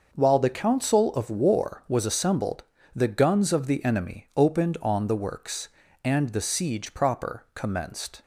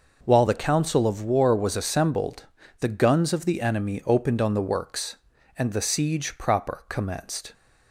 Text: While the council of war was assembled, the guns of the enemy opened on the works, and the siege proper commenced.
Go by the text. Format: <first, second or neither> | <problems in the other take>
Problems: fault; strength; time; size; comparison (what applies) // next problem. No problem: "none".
neither | none